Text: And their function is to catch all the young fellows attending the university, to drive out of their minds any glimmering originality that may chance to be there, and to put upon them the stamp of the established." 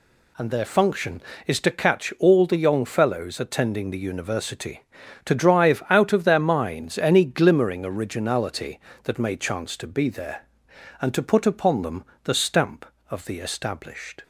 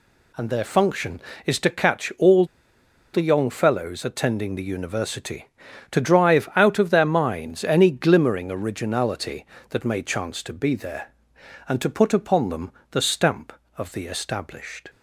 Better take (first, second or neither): first